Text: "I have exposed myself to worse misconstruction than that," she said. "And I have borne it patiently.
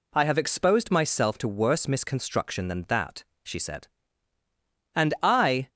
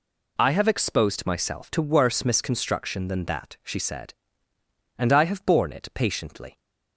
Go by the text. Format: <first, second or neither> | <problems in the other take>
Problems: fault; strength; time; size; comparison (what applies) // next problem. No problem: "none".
second | stops before "have borne it patiently"; at 5.6 s